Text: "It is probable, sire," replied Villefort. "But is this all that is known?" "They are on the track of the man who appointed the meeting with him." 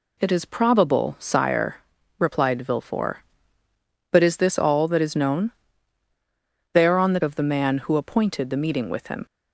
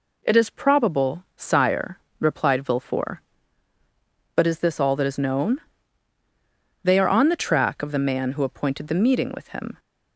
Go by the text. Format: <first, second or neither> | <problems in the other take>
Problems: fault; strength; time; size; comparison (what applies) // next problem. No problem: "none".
second | skips "track"; at 7.2 s